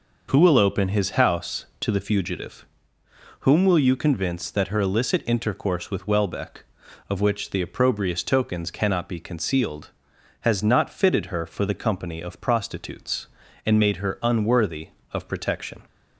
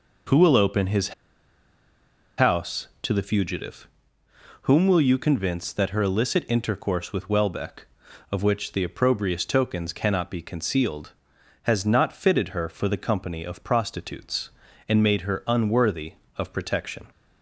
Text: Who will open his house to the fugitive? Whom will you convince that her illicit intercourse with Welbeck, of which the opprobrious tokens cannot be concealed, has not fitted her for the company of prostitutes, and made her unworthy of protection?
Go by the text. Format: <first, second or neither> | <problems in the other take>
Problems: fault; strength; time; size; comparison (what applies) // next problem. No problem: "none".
first | pauses between "his" and "house"; strong; at 1.1 s; 1.2 s long